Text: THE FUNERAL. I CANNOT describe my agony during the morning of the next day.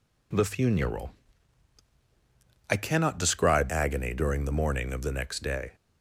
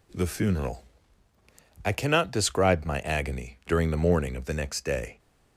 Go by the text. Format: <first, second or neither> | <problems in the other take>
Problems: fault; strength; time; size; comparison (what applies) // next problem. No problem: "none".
second | skips "my"; at 3.6 s